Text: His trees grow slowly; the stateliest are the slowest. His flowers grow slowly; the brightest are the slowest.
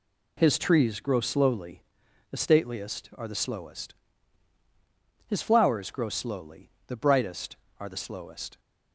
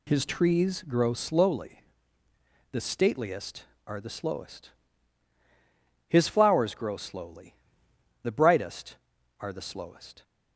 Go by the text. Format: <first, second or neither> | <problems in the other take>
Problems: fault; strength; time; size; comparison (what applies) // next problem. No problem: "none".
neither | none